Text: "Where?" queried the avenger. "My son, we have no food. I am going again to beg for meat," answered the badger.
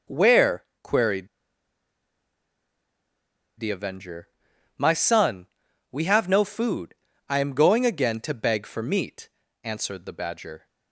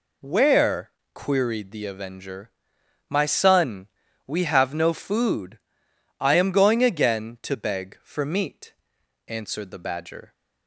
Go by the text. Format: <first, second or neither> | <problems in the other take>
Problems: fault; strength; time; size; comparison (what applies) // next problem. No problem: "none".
second | pauses between "queried" and "the"; strong; at 1.2 s; 2.3 s long